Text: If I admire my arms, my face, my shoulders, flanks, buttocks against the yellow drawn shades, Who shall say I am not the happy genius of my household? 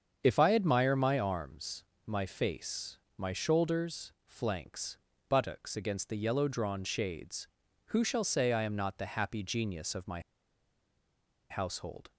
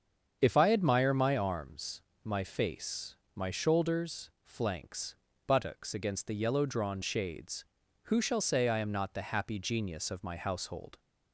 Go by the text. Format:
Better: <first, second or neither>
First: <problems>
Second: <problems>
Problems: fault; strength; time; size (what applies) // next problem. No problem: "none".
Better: second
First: starts louder than the rest; strong; until 1.2 s; 7.5 dB // pauses between "my" and "household"; strong; at 10.1 s; 1.3 s long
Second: starts louder than the rest; strong; until 1.4 s; 7.5 dB